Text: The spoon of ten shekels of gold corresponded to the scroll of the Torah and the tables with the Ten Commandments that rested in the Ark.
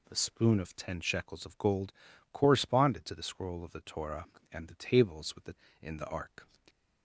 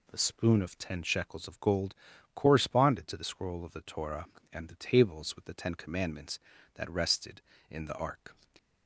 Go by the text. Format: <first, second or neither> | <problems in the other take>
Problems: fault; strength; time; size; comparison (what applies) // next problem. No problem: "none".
second | pauses between "gold" and "corresponded"; at 1.9 s; 0.40 s long; also in the second // skips "Ten Commandments that rested"; at 5.6 s